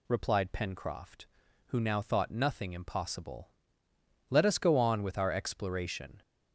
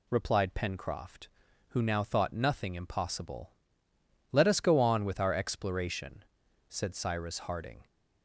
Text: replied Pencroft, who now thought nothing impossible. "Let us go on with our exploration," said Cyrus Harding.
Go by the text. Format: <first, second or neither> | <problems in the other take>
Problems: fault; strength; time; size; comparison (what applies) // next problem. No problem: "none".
second | stops before "said Cyrus Harding"; at 6.2 s